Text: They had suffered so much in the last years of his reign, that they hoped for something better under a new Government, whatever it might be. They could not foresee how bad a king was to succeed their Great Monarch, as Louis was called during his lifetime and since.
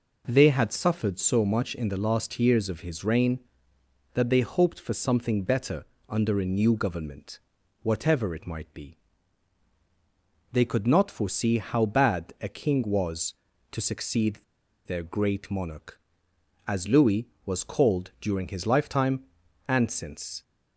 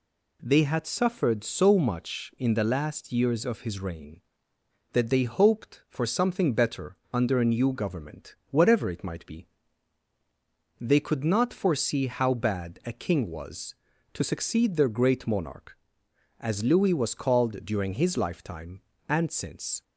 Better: second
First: pauses between "better" and "under"; slight; at 5.8 s; 0.24 s long // pauses between "succeed" and "their"; noticeable; at 14.3 s; 0.48 s long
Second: pauses between "better" and "under"; slight; at 6.9 s; 0.16 s long

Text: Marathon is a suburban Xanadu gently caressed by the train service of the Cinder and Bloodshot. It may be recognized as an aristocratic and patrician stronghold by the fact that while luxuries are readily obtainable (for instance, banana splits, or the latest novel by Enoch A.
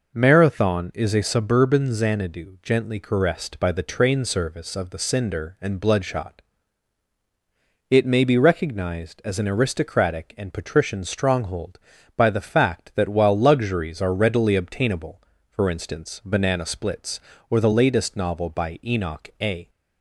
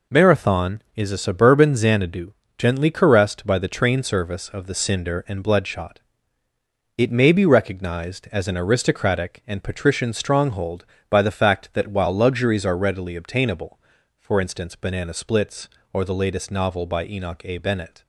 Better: first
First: none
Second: pauses between "Xanadu" and "gently"; slight; at 2.3 s; 0.26 s long // goes on to say "Bennett"; slight; from 17.5 s on; 0.43 s long

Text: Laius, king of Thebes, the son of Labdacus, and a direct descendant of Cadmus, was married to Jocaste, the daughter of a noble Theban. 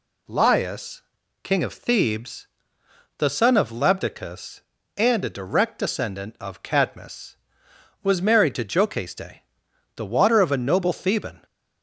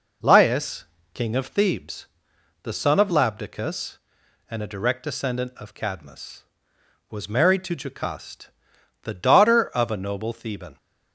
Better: second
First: says "water" for "daughter"; at 10.0 s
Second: none

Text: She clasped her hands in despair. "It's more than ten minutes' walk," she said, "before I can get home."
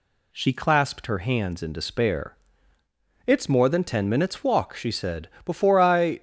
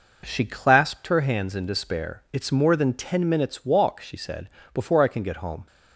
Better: second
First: stops before "can get home"; at 6.1 s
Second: none

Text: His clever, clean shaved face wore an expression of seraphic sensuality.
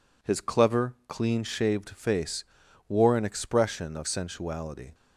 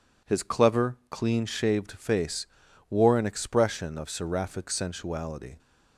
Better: second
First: pauses between "face" and "wore"; at 2.4 s; 0.44 s long // skips "seraphic"; at 4.0 s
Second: pauses between "face" and "wore"; at 2.4 s; 0.43 s long

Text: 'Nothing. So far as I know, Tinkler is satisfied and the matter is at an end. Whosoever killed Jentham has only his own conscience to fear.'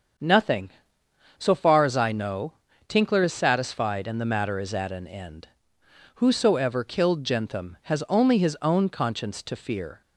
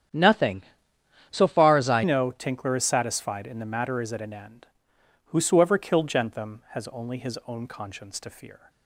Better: first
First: starts louder than the rest; until 1.8 s; 7 dB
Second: starts louder than the rest; strong; until 1.7 s; 9.5 dB // changes voice at "know"; from 2.0 s on; 6.6 s long

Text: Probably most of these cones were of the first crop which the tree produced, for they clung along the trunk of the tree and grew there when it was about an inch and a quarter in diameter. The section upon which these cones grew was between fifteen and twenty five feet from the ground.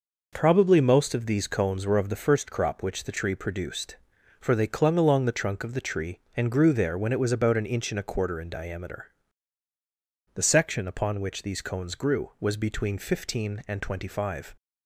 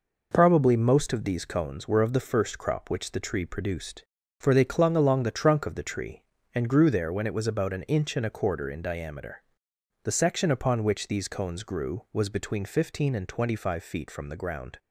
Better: second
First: stops before "feet from the ground"; at 14.5 s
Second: none

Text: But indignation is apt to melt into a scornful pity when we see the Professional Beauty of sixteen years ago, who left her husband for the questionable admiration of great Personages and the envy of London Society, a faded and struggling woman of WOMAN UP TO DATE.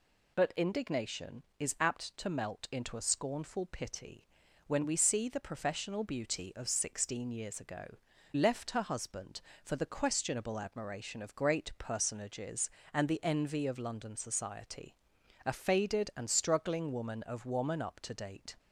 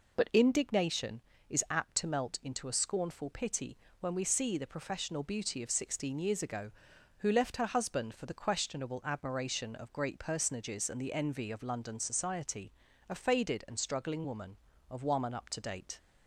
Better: second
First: pauses between "pity" and "when"; at 4.2 s; 0.40 s long // skips "who"; at 8.1 s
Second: pauses between "pity" and "when"; slight; at 3.7 s; 0.24 s long

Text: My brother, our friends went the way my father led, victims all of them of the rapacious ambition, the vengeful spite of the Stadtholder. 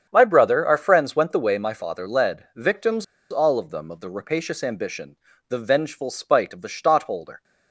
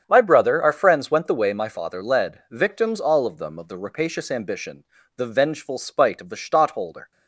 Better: second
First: starts louder than the rest; strong; until 1.1 s; 7.5 dB // pauses between "victims" and "all"; slight; at 3.0 s; 0.26 s long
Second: starts louder than the rest; strong; until 1.0 s; 8 dB

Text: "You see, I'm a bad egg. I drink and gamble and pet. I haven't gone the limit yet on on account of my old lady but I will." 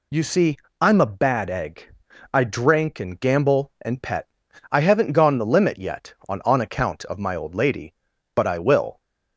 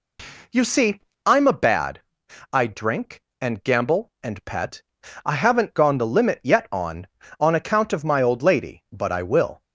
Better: first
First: none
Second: skips "egg"; at 2.2 s

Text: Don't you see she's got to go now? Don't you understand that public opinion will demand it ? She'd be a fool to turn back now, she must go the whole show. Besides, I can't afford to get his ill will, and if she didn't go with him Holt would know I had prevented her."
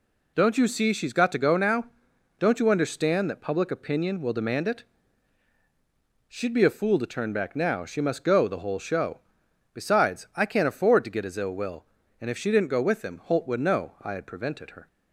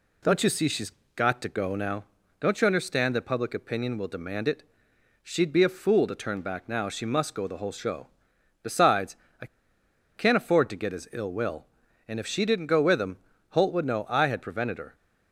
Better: first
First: none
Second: pauses between "she's" and "got"; slight; at 0.9 s; 0.24 s long // pauses between "I" and "can't"; noticeable; at 9.4 s; 0.70 s long // pauses between "him" and "Holt"; slight; at 13.1 s; 0.34 s long

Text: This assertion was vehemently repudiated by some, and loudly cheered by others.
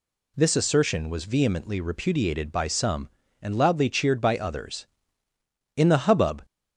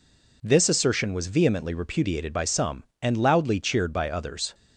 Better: second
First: goes on to say "In the hubbub"; noticeable; from 5.7 s on; 0.68 s long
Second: none

